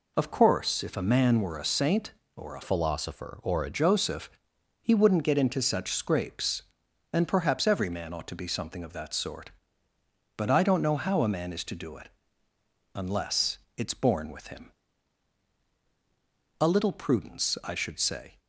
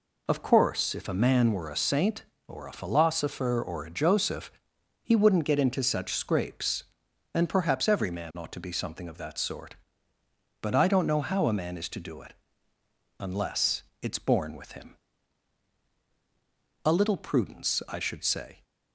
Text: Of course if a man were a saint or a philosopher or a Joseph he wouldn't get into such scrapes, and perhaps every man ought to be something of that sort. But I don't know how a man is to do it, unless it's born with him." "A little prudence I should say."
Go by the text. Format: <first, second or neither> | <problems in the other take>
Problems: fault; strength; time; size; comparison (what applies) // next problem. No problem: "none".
second | changes voice from "philosopher" to "a"; from 2.6 to 3.6 s; 1.0 s long // pauses between "Joseph" and "he"; noticeable; at 4.3 s; 0.50 s long; noticeable in the second // pauses between "unless" and "it's"; slight; at 13.5 s; 0.18 s long; slight in the second